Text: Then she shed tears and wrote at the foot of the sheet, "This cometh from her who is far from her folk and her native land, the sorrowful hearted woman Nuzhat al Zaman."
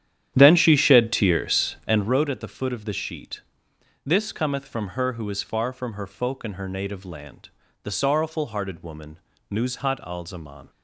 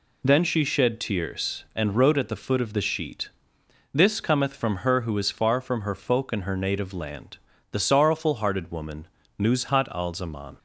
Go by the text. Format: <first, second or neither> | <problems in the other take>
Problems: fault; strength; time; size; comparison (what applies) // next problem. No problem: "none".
second | starts louder than the rest; strong; until 2.1 s; 10.5 dB // pauses between "woman" and "Nuzhat"; slight; at 9.1 s; 0.32 s long; slight in the second